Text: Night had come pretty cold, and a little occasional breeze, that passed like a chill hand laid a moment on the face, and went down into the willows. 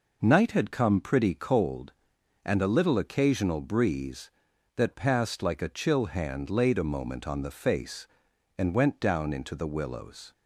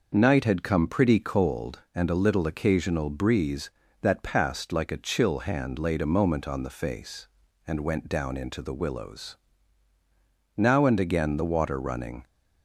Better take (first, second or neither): first